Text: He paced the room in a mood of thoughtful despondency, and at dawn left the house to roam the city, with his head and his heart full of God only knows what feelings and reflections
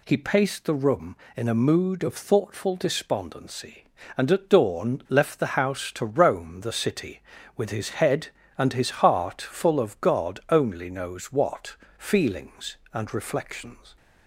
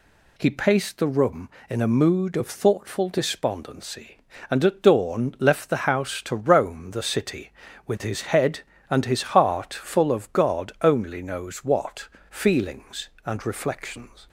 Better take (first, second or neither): neither